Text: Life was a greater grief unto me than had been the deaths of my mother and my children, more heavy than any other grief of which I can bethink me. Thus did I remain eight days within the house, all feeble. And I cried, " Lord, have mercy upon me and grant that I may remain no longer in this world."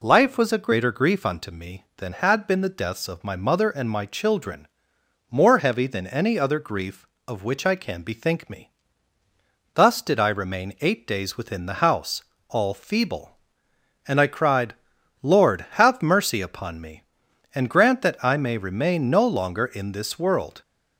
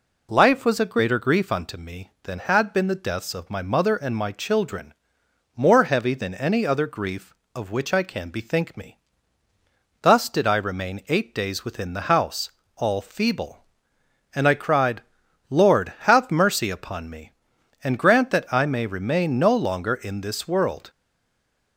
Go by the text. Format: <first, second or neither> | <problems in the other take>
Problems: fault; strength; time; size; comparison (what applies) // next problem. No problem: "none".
first | stays silent after the last word; slight; from 20.8 s on; 0.9 s long